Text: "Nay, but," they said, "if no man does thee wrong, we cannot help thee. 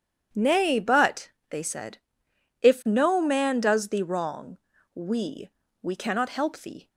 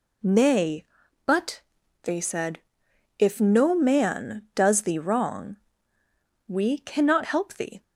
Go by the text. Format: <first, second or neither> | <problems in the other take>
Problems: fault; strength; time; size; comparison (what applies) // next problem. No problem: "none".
second | says "we" twice; at 5.8 s